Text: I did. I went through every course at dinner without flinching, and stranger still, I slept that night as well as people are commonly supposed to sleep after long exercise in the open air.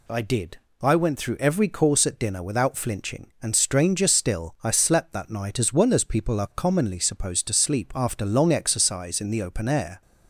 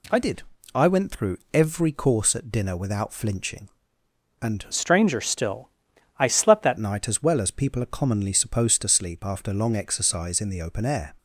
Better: first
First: none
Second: pauses between "through" and "every"; slight; at 1.3 s; 0.16 s long // changes voice from "stranger" to "that"; from 4.7 to 6.7 s; 2.0 s long

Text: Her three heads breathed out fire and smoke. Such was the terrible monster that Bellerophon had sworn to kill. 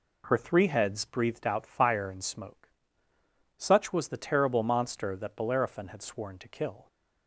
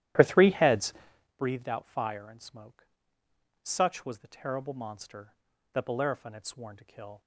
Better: first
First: none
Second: starts louder than the rest; strong; until 1.4 s; 12.5 dB // pauses between "heads" and "breathed"; at 0.9 s; 0.42 s long

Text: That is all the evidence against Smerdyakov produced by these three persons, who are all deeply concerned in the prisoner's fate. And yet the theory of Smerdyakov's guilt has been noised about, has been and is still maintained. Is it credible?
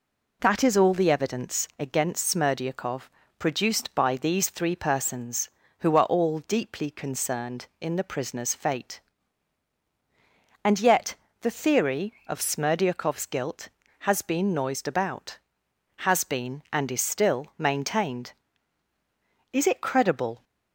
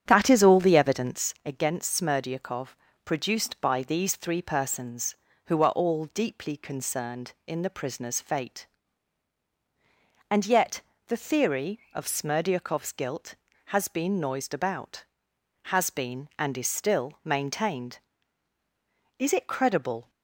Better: first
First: pauses between "Smerdyakov" and "produced"; slight; at 3.0 s; 0.28 s long // pauses between "yet" and "the"; slight; at 11.1 s; 0.26 s long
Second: starts louder than the rest; strong; until 1.3 s; 9 dB // pauses between "Smerdyakov" and "produced"; slight; at 2.7 s; 0.28 s long // pauses between "yet" and "the"; slight; at 10.8 s; 0.26 s long

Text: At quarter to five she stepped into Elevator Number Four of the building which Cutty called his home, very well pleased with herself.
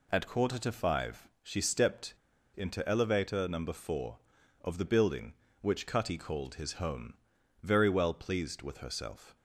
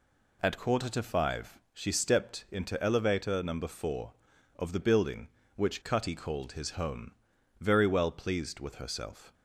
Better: second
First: pauses between "five" and "she"; slight; at 1.2 s; 0.16 s long // pauses between "stepped" and "into"; at 2.1 s; 0.42 s long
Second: pauses between "five" and "she"; slight; at 1.5 s; 0.16 s long

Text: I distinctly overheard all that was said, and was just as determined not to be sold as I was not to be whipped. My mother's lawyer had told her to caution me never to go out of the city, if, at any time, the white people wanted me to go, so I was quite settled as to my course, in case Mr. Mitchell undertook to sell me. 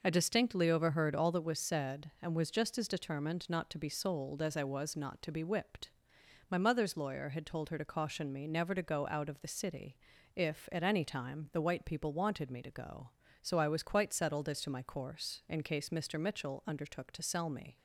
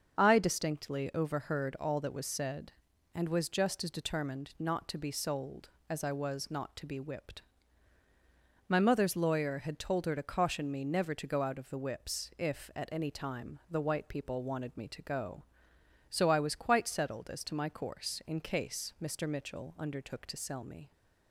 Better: first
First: none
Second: starts louder than the rest; until 1.2 s; 6.5 dB // says "whips" for "city"; at 11.7 s

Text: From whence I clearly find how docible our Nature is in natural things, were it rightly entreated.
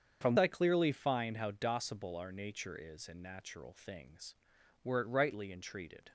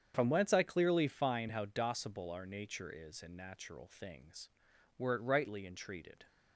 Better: second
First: starts louder than the rest; strong; until 1.2 s; 7 dB // skips "whence"; at 0.3 s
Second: starts louder than the rest; strong; until 1.1 s; 8 dB

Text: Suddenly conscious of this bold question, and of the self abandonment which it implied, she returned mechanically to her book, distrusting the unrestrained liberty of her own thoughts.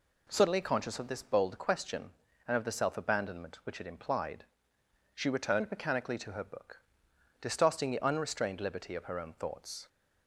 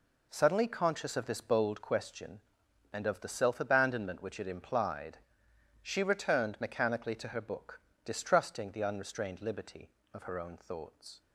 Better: neither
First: none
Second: none

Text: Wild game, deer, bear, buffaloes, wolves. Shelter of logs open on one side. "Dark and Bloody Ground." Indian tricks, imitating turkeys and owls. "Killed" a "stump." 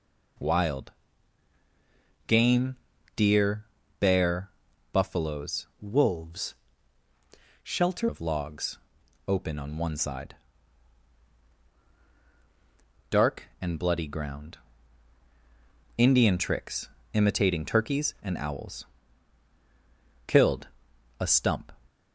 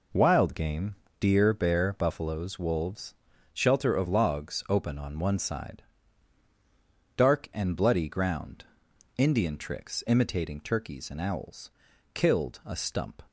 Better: second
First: pauses between "Wild" and "game"; strong; at 0.9 s; 1.3 s long // changes voice from "wolves" to "Shelter"; from 5.7 to 8.0 s; 2.3 s long // pauses between "logs" and "open"; noticeable; at 8.7 s; 0.50 s long // pauses between "Killed" and "a"; noticeable; at 20.6 s; 0.52 s long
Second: none

